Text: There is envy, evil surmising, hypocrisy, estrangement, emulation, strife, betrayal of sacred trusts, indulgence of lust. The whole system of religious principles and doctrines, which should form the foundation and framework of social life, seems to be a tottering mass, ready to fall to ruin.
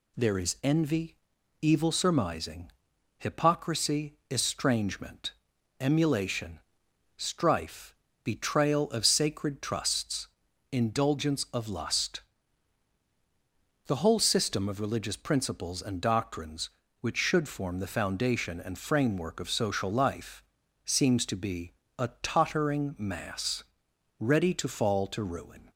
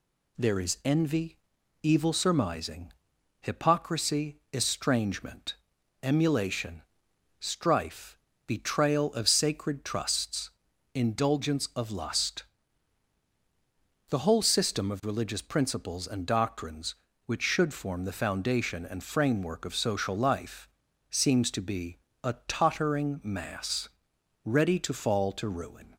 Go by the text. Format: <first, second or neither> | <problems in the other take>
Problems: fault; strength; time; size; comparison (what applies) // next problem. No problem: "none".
neither | pauses between "be" and "a"; slight; the same in both